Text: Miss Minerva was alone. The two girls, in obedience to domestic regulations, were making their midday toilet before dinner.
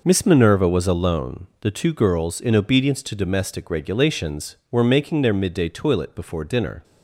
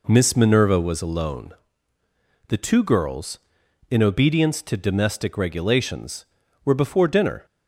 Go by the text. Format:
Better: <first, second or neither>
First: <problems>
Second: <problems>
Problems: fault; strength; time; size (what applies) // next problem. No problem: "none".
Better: first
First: none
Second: skips "making their midday toilet"; at 6.7 s